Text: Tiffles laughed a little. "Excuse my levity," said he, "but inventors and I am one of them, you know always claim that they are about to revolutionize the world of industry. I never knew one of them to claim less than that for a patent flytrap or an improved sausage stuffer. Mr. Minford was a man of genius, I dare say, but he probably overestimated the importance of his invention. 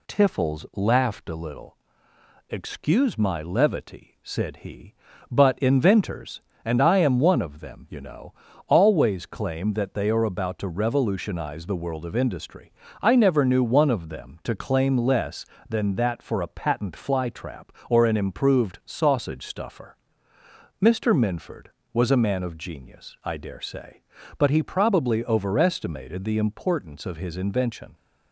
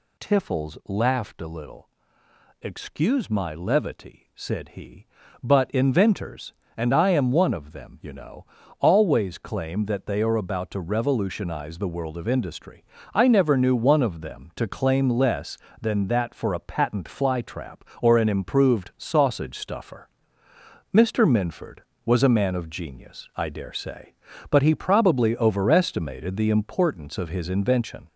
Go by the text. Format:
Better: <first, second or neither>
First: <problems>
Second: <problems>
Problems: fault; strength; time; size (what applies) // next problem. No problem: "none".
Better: first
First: pauses between "know" and "always"; slight; at 8.3 s; 0.34 s long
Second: gets louder; noticeable; throughout; 4 dB // pauses between "know" and "always"; slight; at 8.4 s; 0.34 s long